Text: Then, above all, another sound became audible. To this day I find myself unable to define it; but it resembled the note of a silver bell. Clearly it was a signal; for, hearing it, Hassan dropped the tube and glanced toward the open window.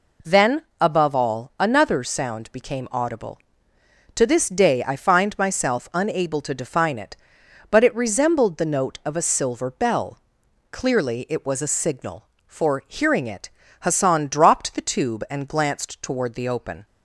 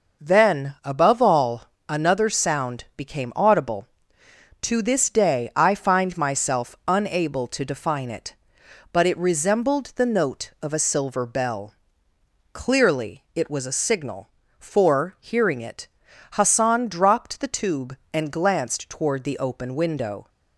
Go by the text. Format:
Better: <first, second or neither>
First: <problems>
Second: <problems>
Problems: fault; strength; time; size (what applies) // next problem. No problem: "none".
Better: second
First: stops before "window"; at 16.8 s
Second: none